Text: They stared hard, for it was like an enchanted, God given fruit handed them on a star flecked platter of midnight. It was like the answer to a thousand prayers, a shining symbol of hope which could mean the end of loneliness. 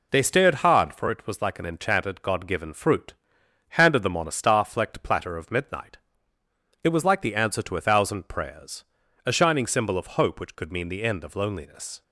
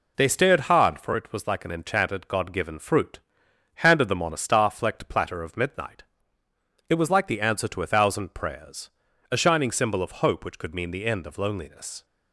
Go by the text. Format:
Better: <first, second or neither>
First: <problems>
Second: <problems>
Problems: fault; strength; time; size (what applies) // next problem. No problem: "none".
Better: neither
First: pauses between "fruit" and "handed"; noticeable; at 3.1 s; 0.60 s long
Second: pauses between "fruit" and "handed"; noticeable; at 3.1 s; 0.60 s long